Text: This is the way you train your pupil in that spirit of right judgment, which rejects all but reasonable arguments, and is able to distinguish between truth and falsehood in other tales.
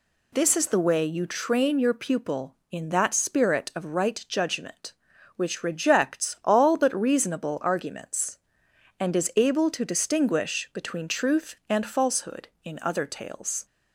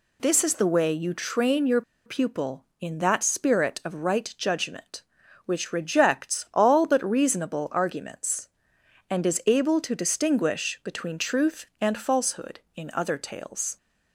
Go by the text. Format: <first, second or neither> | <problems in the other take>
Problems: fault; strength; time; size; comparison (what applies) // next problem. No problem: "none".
first | pauses between "your" and "pupil"; slight; at 1.8 s; 0.25 s long